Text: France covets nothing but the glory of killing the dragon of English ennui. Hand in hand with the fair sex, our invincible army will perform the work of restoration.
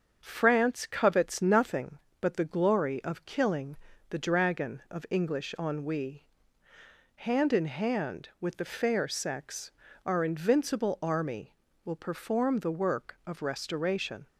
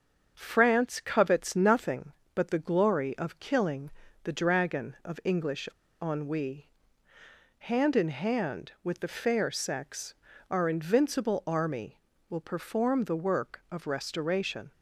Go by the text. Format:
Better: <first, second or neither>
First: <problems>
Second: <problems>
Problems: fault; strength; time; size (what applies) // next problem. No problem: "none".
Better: first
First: starts louder than the rest; until 1.2 s; 7 dB // pauses between "killing" and "the"; slight; at 3.7 s; 0.34 s long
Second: starts louder than the rest; until 1.3 s; 7 dB // pauses between "killing" and "the"; slight; at 3.8 s; 0.34 s long // pauses between "English" and "ennui"; slight; at 5.6 s; 0.35 s long